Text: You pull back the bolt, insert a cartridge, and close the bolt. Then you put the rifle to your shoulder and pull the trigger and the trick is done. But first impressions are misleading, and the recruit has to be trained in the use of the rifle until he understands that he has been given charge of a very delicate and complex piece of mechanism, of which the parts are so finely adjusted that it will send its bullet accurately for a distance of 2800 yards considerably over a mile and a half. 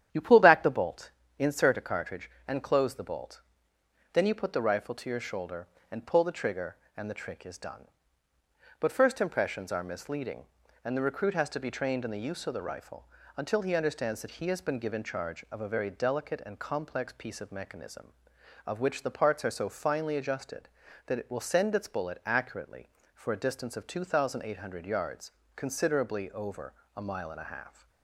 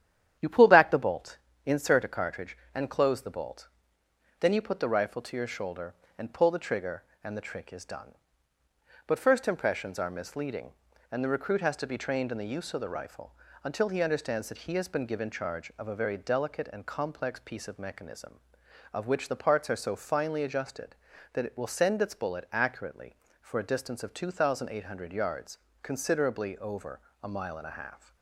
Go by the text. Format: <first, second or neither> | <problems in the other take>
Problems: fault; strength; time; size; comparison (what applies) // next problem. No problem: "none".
neither | starts louder than the rest; strong; the same in both // pauses between "rifle" and "until"; slight; the same in both // pauses between "yards" and "considerably"; slight; the same in both // pauses between "over" and "a"; slight; the same in both